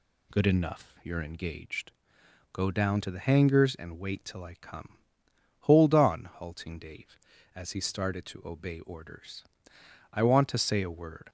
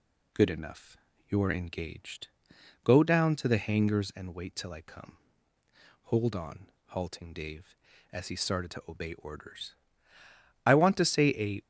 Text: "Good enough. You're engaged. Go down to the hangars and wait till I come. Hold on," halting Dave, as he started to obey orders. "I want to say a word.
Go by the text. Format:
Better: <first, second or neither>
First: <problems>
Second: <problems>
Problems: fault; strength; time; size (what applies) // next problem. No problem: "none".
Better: first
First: none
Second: stops before "word"; at 11.6 s